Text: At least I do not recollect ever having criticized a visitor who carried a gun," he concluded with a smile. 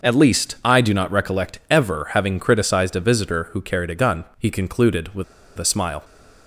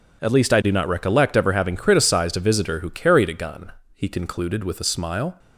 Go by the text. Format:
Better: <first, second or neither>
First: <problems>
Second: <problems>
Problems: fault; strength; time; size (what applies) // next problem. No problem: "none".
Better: second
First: pauses between "with" and "a"; slight; at 5.2 s; 0.34 s long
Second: none